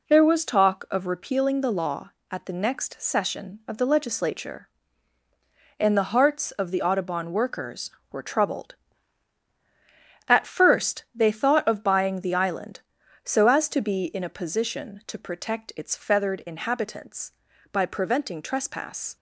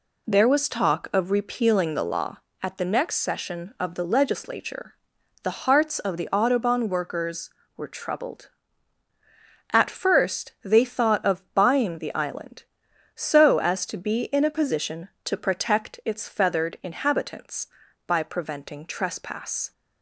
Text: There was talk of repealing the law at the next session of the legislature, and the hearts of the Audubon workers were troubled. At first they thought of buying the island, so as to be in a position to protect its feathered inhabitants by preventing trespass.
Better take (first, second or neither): first